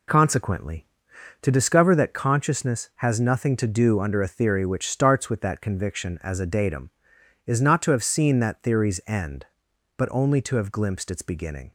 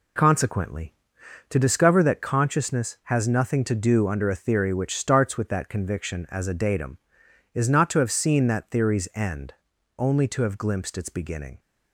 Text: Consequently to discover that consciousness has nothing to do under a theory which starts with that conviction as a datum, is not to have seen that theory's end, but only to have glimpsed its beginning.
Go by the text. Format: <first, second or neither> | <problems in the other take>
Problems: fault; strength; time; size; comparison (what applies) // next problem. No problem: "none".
first | skips "but"; at 9.7 s